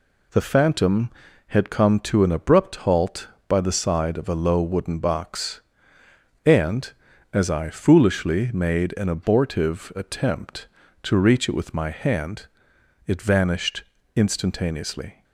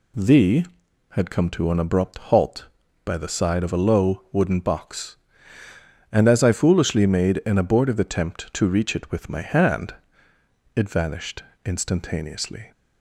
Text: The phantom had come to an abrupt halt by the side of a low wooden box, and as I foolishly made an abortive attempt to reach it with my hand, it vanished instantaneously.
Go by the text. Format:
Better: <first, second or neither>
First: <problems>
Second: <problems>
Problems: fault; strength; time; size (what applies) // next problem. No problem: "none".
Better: first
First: pauses between "vanished" and "instantaneously"; slight; at 13.8 s; 0.32 s long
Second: skips "phantom"; at 0.8 s // pauses between "vanished" and "instantaneously"; slight; at 11.4 s; 0.22 s long